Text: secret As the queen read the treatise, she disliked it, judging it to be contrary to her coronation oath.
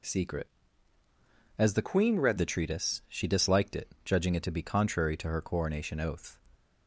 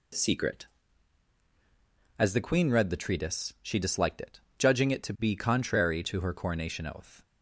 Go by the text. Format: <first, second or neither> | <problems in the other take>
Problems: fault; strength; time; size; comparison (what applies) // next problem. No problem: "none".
second | changes voice from "queen" to "read"; from 1.8 to 2.3 s; 0.5 s long